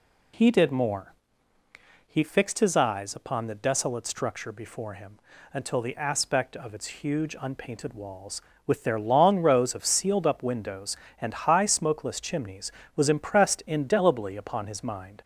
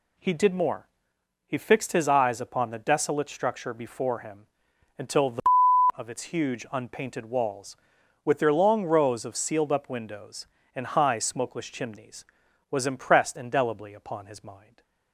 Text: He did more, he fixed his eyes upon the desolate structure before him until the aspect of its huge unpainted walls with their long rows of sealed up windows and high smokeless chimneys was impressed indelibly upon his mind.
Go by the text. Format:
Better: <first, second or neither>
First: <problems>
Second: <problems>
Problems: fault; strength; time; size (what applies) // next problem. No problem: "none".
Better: first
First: pauses between "him" and "until"; slight; at 5.2 s; 0.32 s long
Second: pauses between "him" and "until"; noticeable; at 4.4 s; 0.52 s long // skips "aspect"; at 5.6 s // stays silent after the last word; slight; from 14.5 s on; 0.6 s long